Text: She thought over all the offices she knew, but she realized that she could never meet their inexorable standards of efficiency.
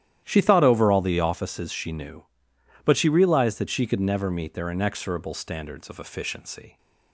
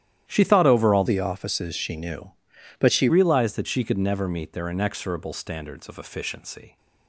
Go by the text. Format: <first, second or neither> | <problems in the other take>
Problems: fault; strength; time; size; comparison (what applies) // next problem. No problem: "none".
first | starts louder than the rest; strong; until 1.2 s; 11.5 dB; strong in the first // changes voice from "the" to "she"; from 1.0 to 3.0 s; 2.0 s long